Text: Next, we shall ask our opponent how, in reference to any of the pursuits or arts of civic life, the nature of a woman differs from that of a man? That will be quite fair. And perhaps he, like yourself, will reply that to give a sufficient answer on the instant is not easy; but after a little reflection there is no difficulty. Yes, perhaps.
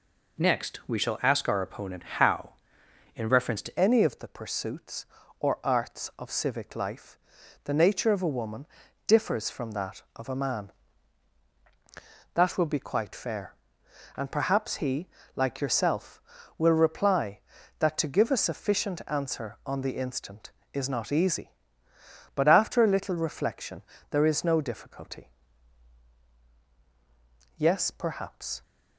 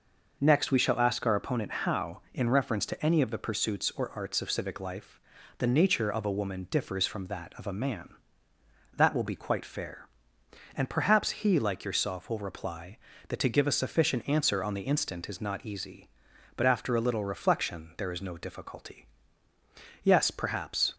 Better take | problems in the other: second | changes voice at "any"; from 3.7 s on; 24.9 s long // pauses between "woman" and "differs"; at 8.6 s; 0.40 s long // pauses between "reflection" and "there"; slight; at 23.8 s; 0.28 s long

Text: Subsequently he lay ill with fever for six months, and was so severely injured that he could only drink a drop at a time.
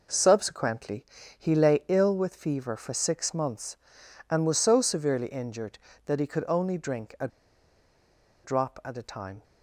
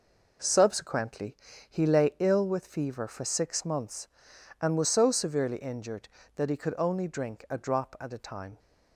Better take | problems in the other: second | pauses between "Subsequently" and "he"; slight; at 1.0 s; 0.32 s long; slight in the second // pauses between "a" and "drop"; at 7.2 s; 1.1 s long

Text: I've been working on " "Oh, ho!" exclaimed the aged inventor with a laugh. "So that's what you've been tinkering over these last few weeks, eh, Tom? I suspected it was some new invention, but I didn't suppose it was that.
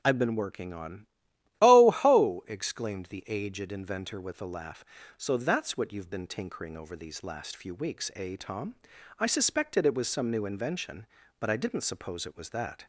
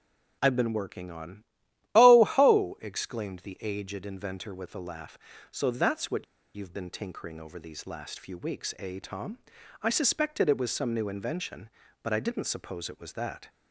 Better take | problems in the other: first | pauses between "what" and "you've"; slight; at 6.2 s; 0.31 s long

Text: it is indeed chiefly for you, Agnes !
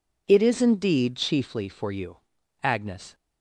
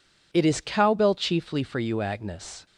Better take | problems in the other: first | says "cowbell" for "indeed"; at 0.6 s

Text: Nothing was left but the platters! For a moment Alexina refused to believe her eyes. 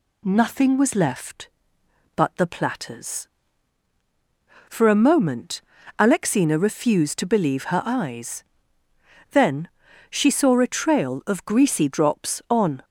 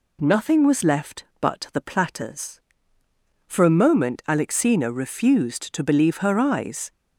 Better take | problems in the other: second | pauses between "moment" and "Alexina"; at 5.5 s; 0.38 s long // goes on to say "Then she saw a trail of greasy drops on"; strong; from 9.3 s on; 3.5 s long

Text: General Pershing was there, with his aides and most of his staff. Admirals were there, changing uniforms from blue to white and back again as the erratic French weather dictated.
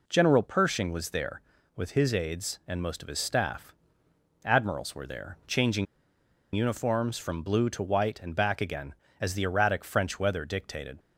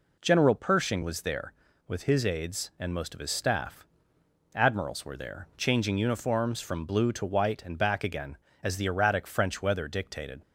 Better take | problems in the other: second | pauses between "changing" and "uniforms"; noticeable; at 5.8 s; 0.69 s long

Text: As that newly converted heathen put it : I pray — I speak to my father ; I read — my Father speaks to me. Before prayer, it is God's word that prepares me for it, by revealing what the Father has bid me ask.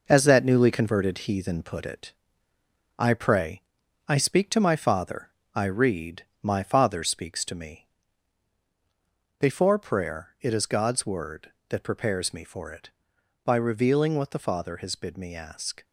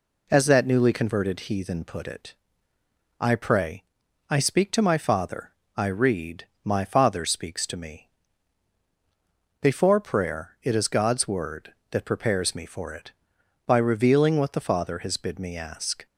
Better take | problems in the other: second | gets quieter; throughout; 7 dB

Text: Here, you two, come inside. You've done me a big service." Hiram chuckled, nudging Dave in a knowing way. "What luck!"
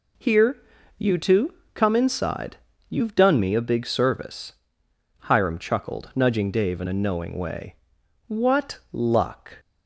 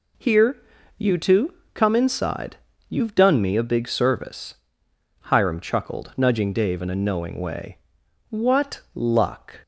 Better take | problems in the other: neither | none

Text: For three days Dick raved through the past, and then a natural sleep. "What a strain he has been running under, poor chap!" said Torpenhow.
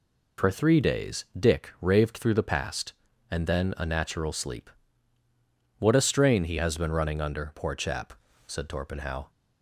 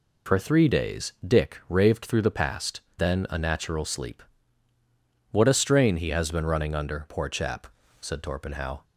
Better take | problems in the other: first | skips "and"; at 2.8 s

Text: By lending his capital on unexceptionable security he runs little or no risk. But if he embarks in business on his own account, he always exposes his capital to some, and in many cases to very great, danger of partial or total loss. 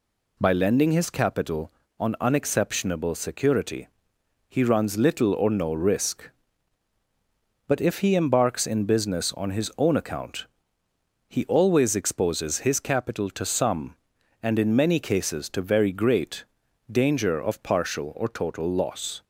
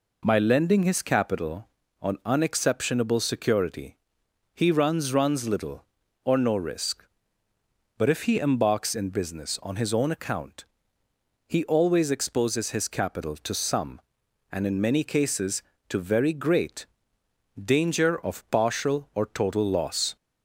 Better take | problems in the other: first | pauses between "security" and "he"; noticeable; at 3.9 s; 0.56 s long; noticeable in the first // says "runs" twice; at 5.1 s

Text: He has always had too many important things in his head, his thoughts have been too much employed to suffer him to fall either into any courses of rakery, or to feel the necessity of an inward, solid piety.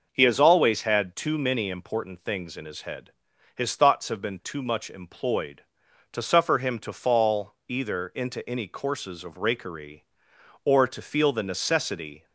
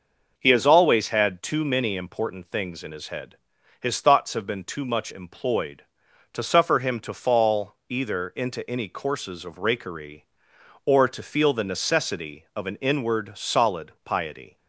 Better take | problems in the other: second | stops before "of an inward solid piety"; at 12.2 s

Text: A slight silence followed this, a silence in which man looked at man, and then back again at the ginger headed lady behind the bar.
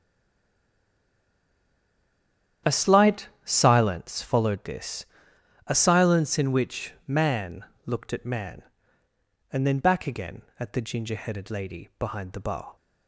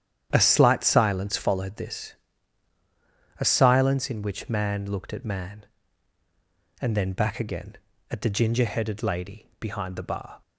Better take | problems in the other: second | stays silent before the first word; strong; until 2.6 s; 2.6 s long // starts louder than the rest; strong; until 3.8 s; 10 dB; strong in the second // pauses between "slight" and "silence"; slight; at 3.2 s; 0.16 s long // pauses between "man" and "looked"; slight; at 7.6 s; 0.20 s long

